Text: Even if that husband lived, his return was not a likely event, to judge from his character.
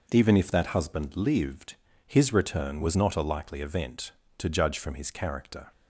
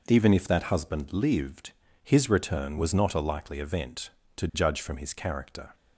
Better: neither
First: none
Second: none

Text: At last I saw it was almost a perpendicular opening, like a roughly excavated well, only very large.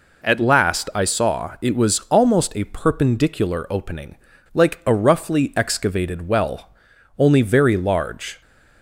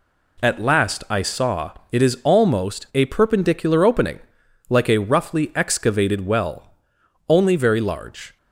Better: first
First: none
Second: pauses between "saw" and "it"; slight; at 1.7 s; 0.18 s long // says "is" for "was"; at 2.0 s

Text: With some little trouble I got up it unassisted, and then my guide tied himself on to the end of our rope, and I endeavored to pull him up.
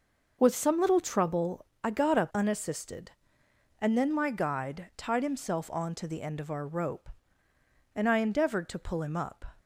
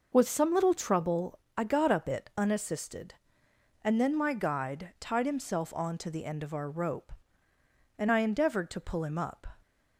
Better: second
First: pauses between "trouble" and "I"; slight; at 1.6 s; 0.18 s long // skips "it"; at 2.3 s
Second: pauses between "trouble" and "I"; slight; at 1.3 s; 0.18 s long

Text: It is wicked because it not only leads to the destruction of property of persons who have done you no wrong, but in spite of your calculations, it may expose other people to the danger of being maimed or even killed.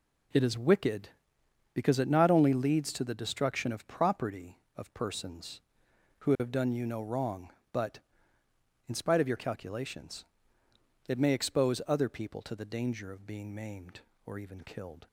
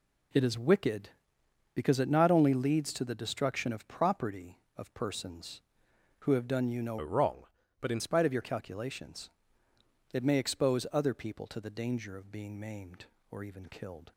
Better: first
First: none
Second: changes voice from "wrong" to "in"; from 7.0 to 8.0 s; 1.0 s long

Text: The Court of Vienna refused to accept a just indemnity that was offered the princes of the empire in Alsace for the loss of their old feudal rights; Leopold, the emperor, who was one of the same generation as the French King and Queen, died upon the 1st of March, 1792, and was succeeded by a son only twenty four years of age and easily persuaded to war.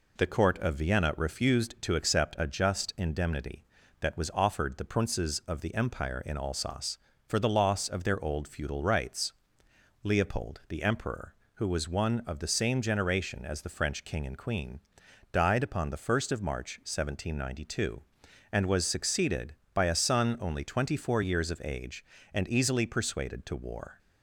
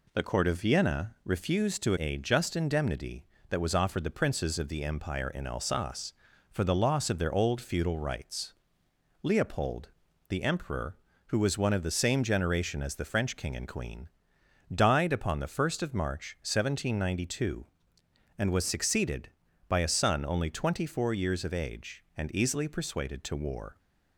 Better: first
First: none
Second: skips "accept"; at 1.9 s

